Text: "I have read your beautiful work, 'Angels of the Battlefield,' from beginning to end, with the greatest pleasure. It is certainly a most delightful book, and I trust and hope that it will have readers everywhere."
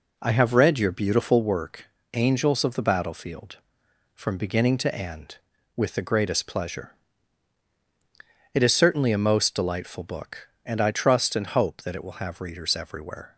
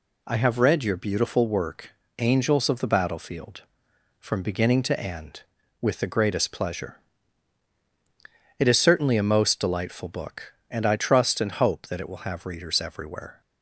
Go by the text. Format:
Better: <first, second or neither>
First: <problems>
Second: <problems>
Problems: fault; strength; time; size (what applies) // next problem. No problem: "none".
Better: second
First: starts louder than the rest; until 1.5 s; 3.5 dB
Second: none